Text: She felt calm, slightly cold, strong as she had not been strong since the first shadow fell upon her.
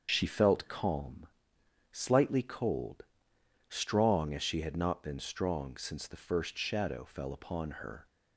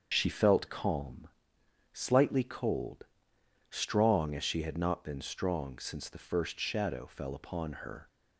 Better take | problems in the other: neither | starts louder than the rest; the same in both

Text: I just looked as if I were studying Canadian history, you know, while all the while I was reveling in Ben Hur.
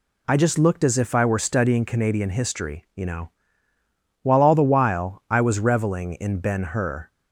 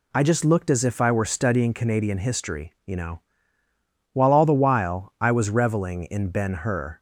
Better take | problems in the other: neither | none

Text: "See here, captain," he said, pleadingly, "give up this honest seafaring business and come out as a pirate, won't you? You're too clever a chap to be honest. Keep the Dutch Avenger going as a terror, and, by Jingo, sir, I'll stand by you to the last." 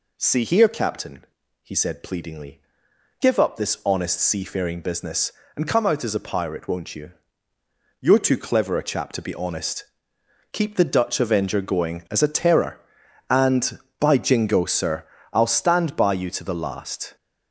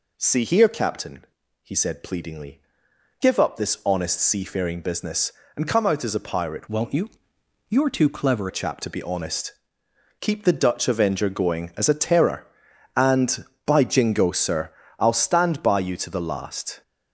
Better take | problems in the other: first | changes voice from "won't" to "clever"; from 6.6 to 8.4 s; 1.8 s long

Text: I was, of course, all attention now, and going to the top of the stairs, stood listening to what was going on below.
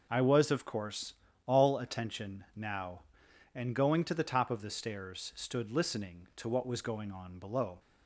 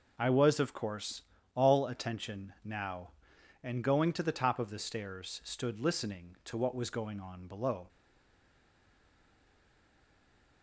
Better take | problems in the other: first | stays silent after the last word; strong; from 7.8 s on; 2.8 s long

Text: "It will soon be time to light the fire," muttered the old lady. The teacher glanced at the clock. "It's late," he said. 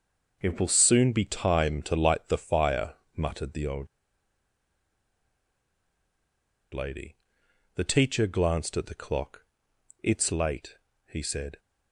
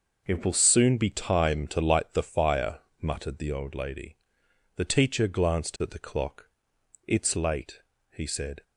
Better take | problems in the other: second | pauses between "old" and "lady"; strong; at 3.8 s; 2.8 s long

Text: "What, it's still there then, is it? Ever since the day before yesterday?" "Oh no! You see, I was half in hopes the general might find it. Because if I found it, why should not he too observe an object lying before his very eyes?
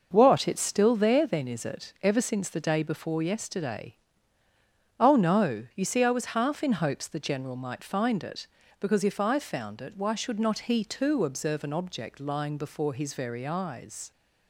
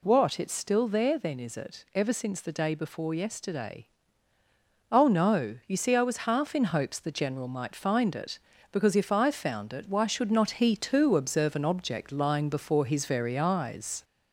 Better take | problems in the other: first | gets louder; slight; throughout; 2.5 dB

